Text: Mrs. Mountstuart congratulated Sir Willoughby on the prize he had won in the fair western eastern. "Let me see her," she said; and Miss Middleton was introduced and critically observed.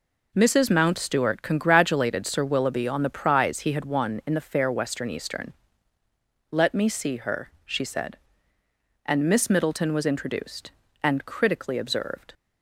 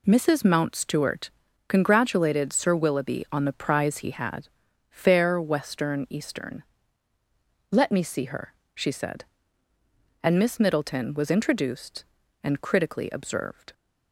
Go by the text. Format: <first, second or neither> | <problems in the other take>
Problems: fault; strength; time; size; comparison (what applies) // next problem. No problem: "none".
first | pauses between "Mountstuart" and "congratulated"; slight; at 1.3 s; 0.36 s long // skips "won in the"; at 4.6 s